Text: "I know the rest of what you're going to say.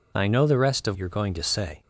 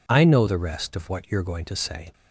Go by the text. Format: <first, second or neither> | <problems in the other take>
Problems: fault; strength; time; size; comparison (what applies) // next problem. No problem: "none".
second | skips "what"; at 0.9 s